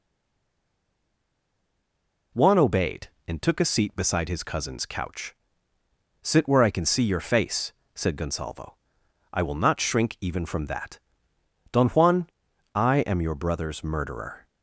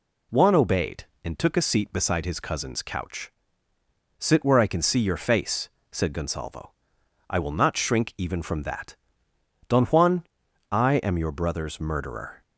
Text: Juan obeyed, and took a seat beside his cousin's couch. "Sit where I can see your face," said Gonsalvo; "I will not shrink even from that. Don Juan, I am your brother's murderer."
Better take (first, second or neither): second